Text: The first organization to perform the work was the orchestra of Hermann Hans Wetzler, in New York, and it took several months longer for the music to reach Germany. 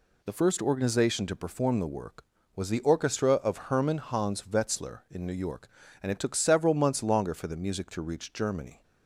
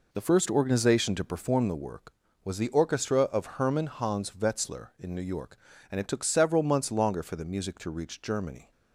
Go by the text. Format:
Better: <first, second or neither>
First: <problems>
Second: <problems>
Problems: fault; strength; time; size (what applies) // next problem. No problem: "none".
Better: first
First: none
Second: starts louder than the rest; noticeable; until 1.7 s; 4 dB